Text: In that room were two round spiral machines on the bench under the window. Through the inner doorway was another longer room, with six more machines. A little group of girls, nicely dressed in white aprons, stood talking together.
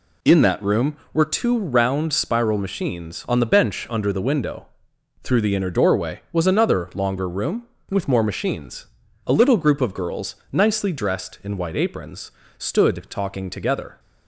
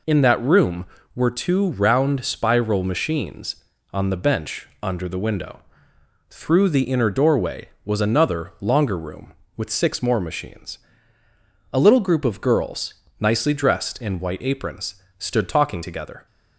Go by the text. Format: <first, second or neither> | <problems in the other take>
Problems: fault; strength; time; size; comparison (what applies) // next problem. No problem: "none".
second | skips "six"; at 8.0 s